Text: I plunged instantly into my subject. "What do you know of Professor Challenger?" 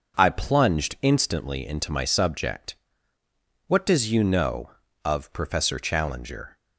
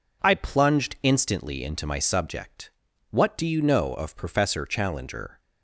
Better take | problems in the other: second | says "does" for "do"; at 3.8 s

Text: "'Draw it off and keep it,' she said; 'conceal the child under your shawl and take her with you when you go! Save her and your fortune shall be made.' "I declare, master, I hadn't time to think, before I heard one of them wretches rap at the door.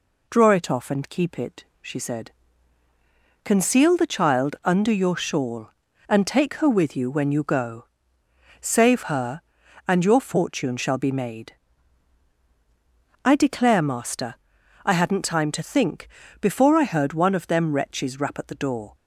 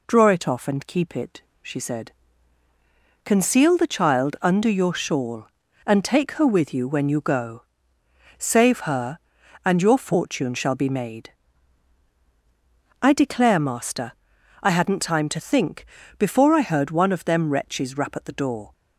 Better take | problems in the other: neither | none

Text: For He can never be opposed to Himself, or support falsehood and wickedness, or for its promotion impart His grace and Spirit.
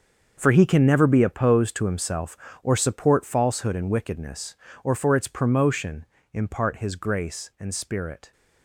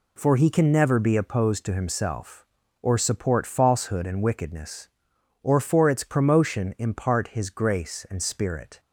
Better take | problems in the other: second | gets quieter; strong; throughout; 13.5 dB // pauses between "promotion" and "impart"; slight; at 6.0 s; 0.26 s long

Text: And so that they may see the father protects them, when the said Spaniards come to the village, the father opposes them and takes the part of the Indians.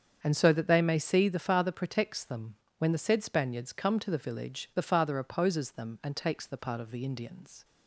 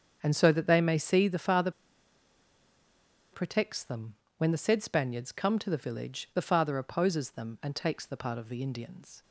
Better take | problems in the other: first | starts louder than the rest; strong; until 1.2 s; 7.5 dB; strong in the first // pauses between "father" and "protects"; strong; at 1.7 s; 1.6 s long

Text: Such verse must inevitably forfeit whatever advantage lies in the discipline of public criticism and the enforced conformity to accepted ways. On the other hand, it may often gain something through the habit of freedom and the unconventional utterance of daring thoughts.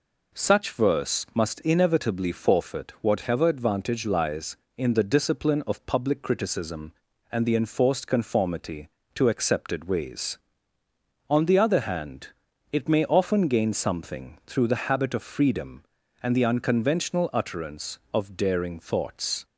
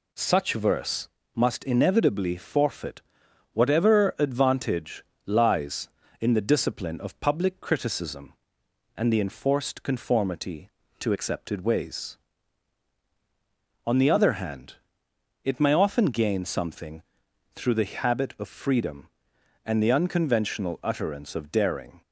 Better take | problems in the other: first | pauses between "verse" and "must"; slight; at 1.0 s; 0.26 s long // pauses between "forfeit" and "whatever"; noticeable; at 3.0 s; 0.52 s long // pauses between "advantage" and "lies"; slight; at 5.0 s; 0.22 s long // pauses between "something" and "through"; noticeable; at 17.0 s; 0.52 s long // stops before "thoughts"; at 22.0 s

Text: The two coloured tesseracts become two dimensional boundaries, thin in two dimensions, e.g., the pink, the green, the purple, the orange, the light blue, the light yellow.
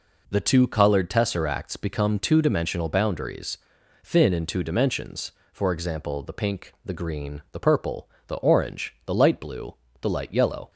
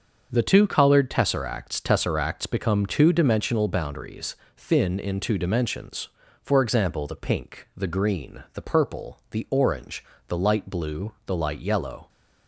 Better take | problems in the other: first | starts louder than the rest; until 1.3 s; 7 dB // says "tesseracts" twice; at 1.8 s

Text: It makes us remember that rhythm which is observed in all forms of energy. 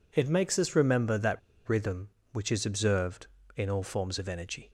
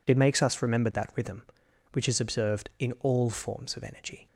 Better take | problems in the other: second | pauses between "that" and "rhythm"; slight; at 1.3 s; 0.27 s long

